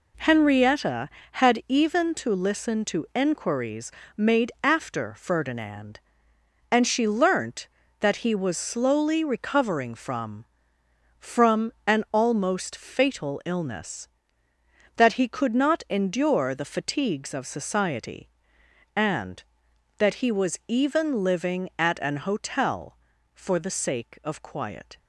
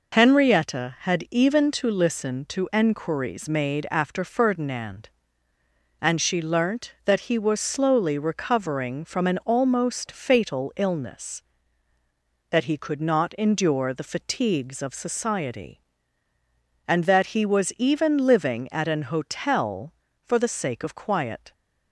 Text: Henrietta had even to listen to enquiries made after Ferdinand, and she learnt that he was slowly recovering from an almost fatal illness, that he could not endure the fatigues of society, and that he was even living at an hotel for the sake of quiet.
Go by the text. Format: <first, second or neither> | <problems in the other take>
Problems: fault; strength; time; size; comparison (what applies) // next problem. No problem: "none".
second | pauses between "enquiries" and "made"; slight; at 3.9 s; 0.24 s long // says "from" twice; at 11.1 s